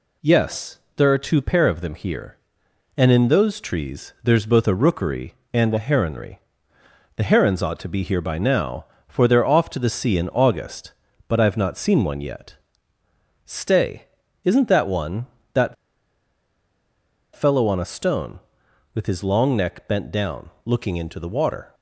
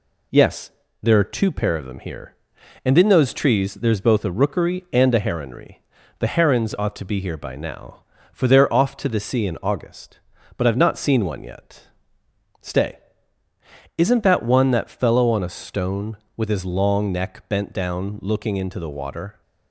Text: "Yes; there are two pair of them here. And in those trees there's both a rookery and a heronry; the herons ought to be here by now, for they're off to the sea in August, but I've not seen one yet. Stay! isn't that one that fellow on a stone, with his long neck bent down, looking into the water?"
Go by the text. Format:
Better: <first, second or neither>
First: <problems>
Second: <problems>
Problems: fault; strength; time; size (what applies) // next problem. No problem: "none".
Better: second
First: pauses between "that" and "fellow"; strong; at 15.7 s; 1.6 s long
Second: none